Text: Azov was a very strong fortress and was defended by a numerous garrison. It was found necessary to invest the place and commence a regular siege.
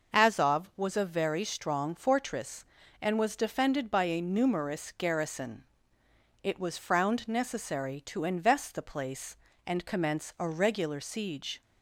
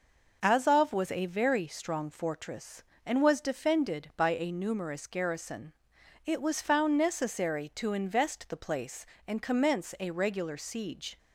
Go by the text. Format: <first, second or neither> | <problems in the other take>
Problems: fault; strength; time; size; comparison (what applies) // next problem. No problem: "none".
second | says "frowned" for "found"; at 6.7 s